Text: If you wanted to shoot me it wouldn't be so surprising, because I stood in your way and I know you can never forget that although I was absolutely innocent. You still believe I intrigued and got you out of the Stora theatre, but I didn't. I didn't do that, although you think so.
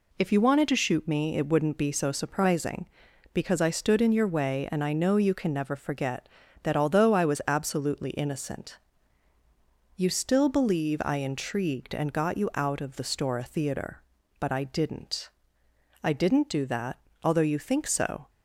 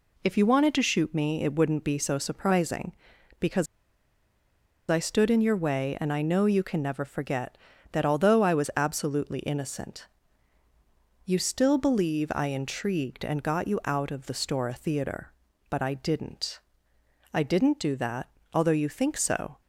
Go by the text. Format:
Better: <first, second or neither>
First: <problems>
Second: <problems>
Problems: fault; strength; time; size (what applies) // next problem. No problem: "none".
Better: first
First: none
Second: pauses between "because" and "I"; at 3.6 s; 1.2 s long